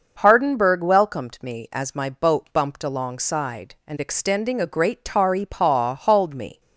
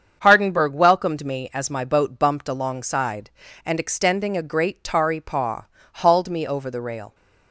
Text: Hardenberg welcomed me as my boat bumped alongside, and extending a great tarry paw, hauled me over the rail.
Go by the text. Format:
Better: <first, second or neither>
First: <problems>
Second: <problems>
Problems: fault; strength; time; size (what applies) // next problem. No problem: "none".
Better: second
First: starts louder than the rest; noticeable; until 1.2 s; 6 dB // stops before "over the rail"; at 6.5 s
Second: starts louder than the rest; strong; until 1.2 s; 7 dB